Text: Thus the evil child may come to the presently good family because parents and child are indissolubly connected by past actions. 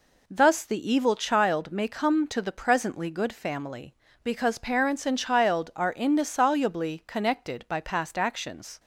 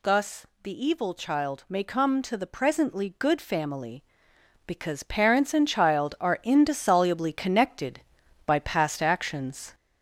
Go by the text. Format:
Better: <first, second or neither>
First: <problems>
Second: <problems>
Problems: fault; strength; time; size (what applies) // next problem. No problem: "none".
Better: first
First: none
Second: gets louder; throughout; 3.5 dB // pauses between "Thus" and "the"; slight; at 0.4 s; 0.16 s long